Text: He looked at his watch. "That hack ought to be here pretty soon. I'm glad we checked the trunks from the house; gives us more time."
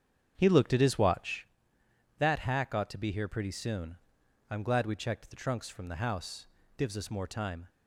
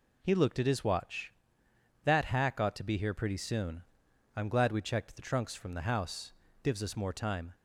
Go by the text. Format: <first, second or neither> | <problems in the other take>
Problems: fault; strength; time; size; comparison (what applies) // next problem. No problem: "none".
second | starts louder than the rest; strong; until 1.5 s; 8 dB